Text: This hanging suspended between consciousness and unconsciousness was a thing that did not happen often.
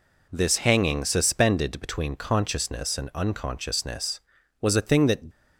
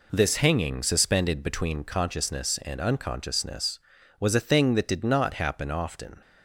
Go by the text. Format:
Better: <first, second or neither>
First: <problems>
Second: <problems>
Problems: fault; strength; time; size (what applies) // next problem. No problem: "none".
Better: second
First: stops before "did not happen often"; at 5.3 s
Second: none